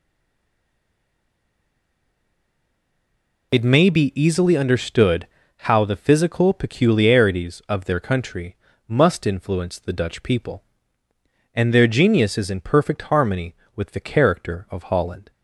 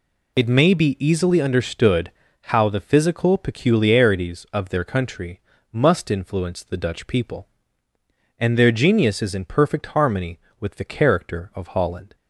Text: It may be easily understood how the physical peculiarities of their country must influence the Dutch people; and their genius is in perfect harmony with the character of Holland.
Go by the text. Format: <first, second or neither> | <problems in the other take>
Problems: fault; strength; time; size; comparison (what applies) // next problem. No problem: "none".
second | stays silent before the first word; strong; until 3.5 s; 3.5 s long // pauses between "understood" and "how"; slight; at 5.2 s; 0.36 s long; slight in the second // pauses between "country" and "must"; slight; at 8.5 s; 0.32 s long; slight in the second